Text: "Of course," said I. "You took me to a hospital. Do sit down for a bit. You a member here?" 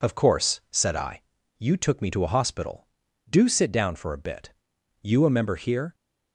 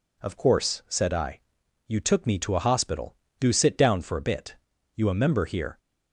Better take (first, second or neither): neither